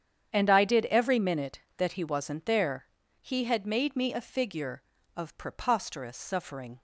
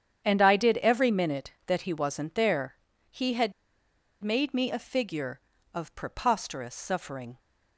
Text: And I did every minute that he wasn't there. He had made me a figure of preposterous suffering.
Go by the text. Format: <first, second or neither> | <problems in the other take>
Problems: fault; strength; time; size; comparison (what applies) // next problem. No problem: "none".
first | starts louder than the rest; strong; until 1.2 s; 9 dB; strong in the first // pauses between "had" and "made"; noticeable; at 3.5 s; 0.71 s long